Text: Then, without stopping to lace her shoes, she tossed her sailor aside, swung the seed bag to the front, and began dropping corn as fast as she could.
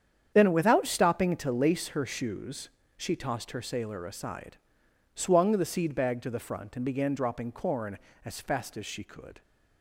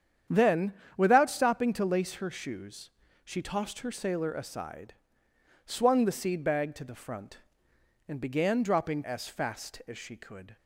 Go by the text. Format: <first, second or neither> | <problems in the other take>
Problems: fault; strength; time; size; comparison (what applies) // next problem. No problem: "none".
first | starts louder than the rest; strong; until 1.5 s; 9 dB; strong in the first // skips "corn"; at 9.0 s